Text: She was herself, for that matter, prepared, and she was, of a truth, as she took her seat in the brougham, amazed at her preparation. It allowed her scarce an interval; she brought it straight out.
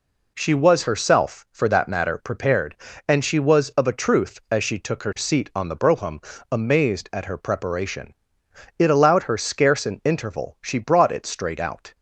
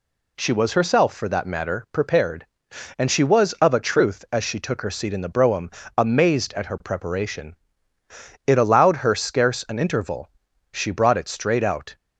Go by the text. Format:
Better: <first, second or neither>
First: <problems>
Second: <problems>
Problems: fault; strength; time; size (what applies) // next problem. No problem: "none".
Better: second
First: says "on" for "in"; at 5.5 s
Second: none